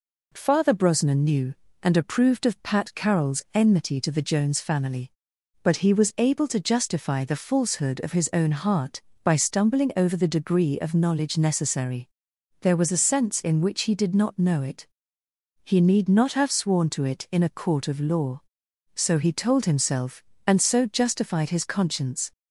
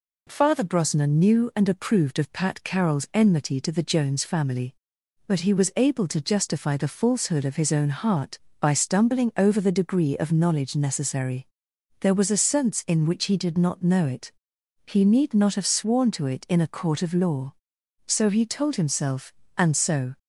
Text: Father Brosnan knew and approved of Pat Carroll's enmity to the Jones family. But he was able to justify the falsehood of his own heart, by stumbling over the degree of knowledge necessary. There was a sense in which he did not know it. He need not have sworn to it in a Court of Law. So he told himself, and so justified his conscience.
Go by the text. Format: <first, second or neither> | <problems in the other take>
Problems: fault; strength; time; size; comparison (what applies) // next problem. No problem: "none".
first | stops before "justified his conscience"; at 20.1 s